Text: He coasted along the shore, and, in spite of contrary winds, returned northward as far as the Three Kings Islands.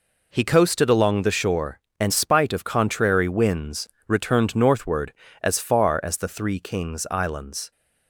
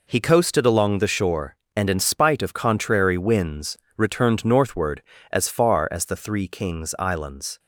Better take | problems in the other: second | skips "in"; at 2.1 s

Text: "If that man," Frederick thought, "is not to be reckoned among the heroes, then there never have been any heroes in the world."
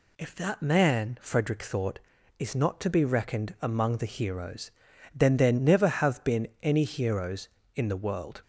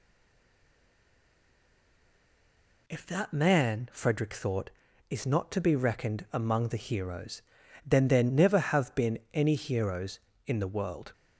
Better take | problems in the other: first | stays silent before the first word; strong; until 2.8 s; 2.8 s long // pauses between "been" and "any"; slight; at 9.1 s; 0.16 s long; slight in the first

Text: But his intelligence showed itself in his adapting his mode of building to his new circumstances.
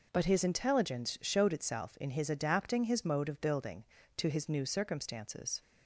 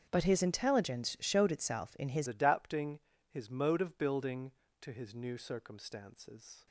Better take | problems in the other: first | starts louder than the rest; strong; until 1.1 s; 7.5 dB // changes voice at "adapting"; from 2.2 s on; 4.4 s long // pauses between "adapting" and "his"; slight; at 2.9 s; 0.30 s long

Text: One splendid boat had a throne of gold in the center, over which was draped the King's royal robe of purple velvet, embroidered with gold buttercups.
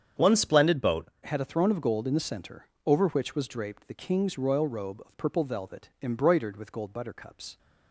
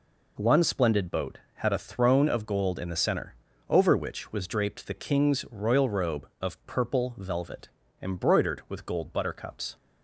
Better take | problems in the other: second | starts louder than the rest; strong; until 1.3 s; 8 dB // changes voice at "had"; from 1.2 s on; 6.3 s long

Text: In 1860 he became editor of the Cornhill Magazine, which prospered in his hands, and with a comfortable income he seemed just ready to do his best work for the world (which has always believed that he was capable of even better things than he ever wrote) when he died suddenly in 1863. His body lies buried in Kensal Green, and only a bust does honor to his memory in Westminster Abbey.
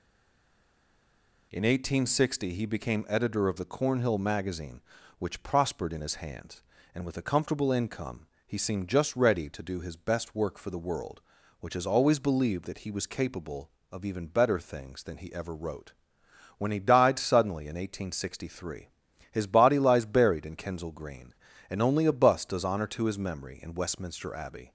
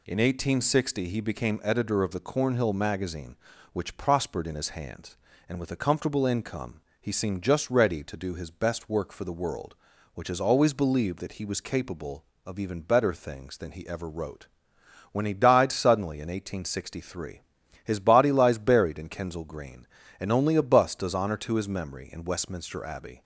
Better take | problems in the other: second | stays silent before the first word; noticeable; until 1.5 s; 1.5 s long // pauses between "income" and "he"; slight; at 8.2 s; 0.22 s long; slight in the second

